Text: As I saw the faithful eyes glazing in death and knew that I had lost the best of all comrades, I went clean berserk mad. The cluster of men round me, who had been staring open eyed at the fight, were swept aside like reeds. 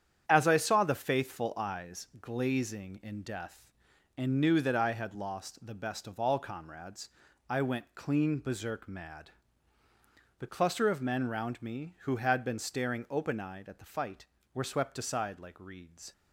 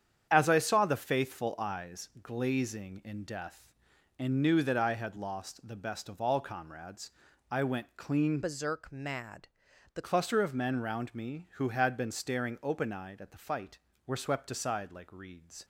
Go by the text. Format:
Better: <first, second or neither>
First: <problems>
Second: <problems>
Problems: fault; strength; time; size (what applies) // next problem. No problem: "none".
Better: first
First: starts louder than the rest; strong; until 1.2 s; 9 dB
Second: starts louder than the rest; strong; until 1.3 s; 8.5 dB // changes voice from "berserk" to "The"; from 8.4 to 10.0 s; 1.6 s long